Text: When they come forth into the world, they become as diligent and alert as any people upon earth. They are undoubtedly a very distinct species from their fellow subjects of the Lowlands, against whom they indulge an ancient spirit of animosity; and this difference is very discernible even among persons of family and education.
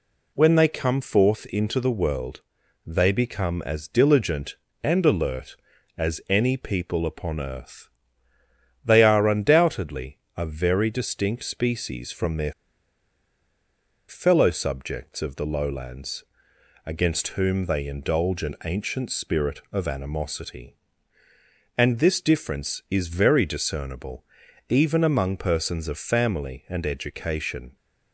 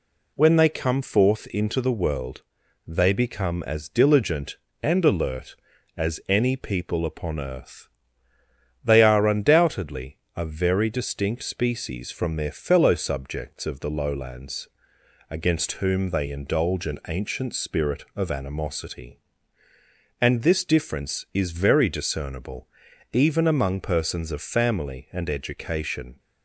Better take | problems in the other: second | pauses between "undoubtedly" and "a"; slight; at 10.1 s; 0.18 s long; slight in the second // pauses between "their" and "fellow"; strong; at 12.5 s; 1.5 s long // pauses between "discernible" and "even"; at 24.2 s; 0.44 s long; also in the second

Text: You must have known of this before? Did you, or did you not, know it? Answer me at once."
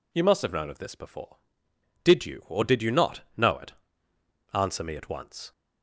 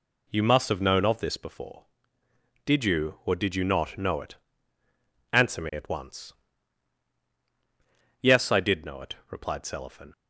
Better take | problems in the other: first | goes on to say "Yes I did know it replied Selifan"; strong; from 8.2 s on; 1.9 s long

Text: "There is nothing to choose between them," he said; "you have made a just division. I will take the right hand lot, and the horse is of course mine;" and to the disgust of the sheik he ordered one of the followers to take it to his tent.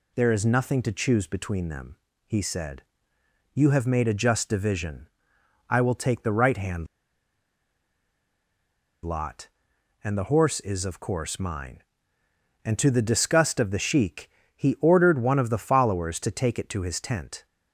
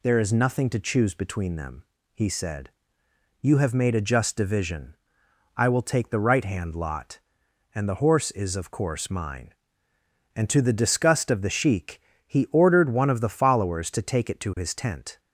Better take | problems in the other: second | pauses between "hand" and "lot"; strong; at 6.8 s; 2.1 s long // pauses between "sheik" and "he"; slight; at 14.2 s; 0.28 s long; slight in the second

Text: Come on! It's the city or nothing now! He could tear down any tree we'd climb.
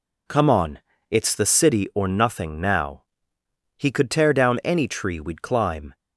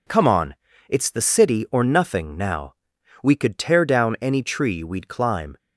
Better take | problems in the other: first | says "We" for "He"; at 3.2 s

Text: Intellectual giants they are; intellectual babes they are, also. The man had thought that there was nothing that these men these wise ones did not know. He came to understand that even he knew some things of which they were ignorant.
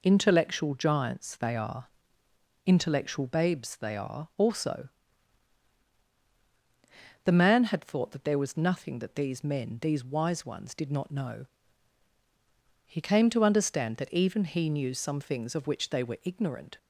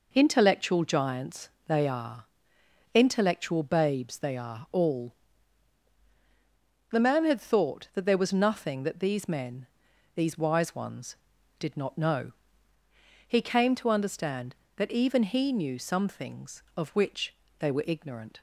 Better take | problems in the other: first | pauses between "giants" and "they"; slight; at 1.5 s; 0.18 s long // says "all" for "also"; at 4.7 s // pauses between "men" and "these"; noticeable; at 9.6 s; 0.48 s long // pauses between "which" and "they"; slight; at 17.3 s; 0.26 s long

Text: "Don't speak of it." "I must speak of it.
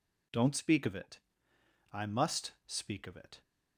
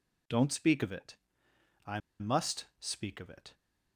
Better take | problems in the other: first | pauses between "I" and "must"; slight; at 1.9 s; 0.20 s long

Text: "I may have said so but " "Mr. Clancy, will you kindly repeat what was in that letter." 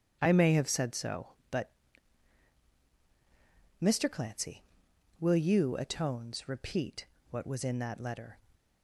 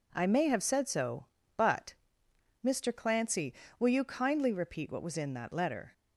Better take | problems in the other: second | starts louder than the rest; until 1.2 s; 6.5 dB // says "atones" for "kindly"; at 5.7 s // pauses between "repeat" and "what"; slight; at 7.0 s; 0.24 s long

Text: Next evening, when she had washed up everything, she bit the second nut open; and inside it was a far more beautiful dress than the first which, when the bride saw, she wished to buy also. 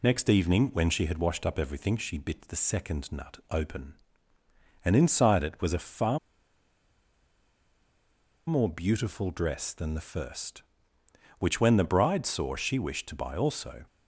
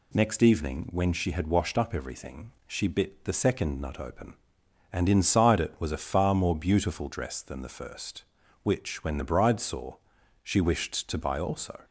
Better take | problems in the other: second | pauses between "far" and "more"; strong; at 6.1 s; 2.2 s long

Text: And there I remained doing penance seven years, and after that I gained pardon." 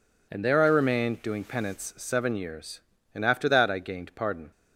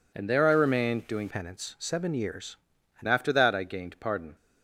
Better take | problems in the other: first | changes voice from "penance" to "and"; from 1.2 to 3.0 s; 1.8 s long

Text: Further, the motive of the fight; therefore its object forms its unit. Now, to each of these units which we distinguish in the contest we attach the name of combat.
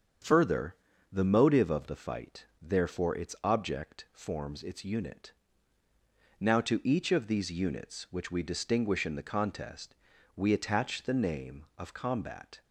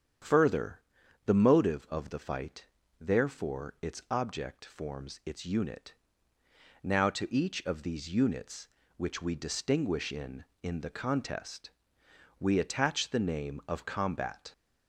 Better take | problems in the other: first | starts louder than the rest; strong; until 1.6 s; 8.5 dB; strong in the first // says "in" twice; at 10.6 s // pauses between "contest" and "we"; noticeable; at 11.7 s; 0.68 s long; also in the first

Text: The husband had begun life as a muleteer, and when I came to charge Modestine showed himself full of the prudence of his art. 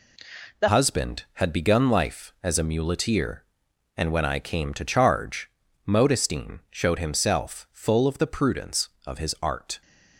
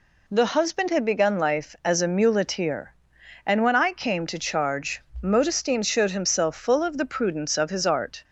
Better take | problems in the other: second | changes voice at "husband"; from 0.6 s on; 9.2 s long // pauses between "charge" and "Modestine"; at 5.4 s; 0.38 s long; slight in the second

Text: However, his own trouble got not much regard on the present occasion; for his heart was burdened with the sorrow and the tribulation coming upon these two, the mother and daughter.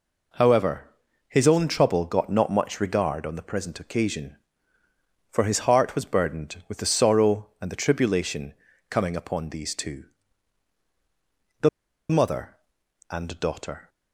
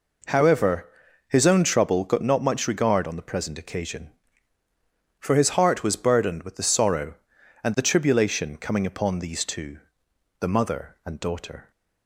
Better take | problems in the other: second | pauses between "tribulation" and "coming"; slight; at 8.5 s; 0.36 s long // pauses between "the" and "mother"; at 11.6 s; 0.41 s long

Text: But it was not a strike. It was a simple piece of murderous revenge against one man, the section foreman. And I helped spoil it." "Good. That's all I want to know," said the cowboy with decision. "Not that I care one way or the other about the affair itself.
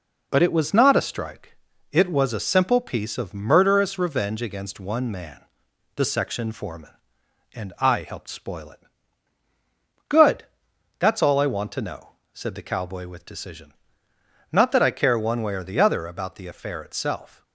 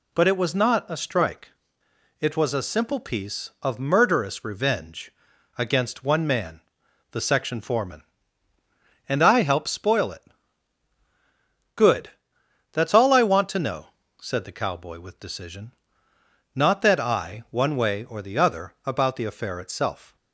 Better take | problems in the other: first | pauses between "revenge" and "against"; noticeable; at 5.1 s; 0.46 s long // skips "care"; at 17.4 s

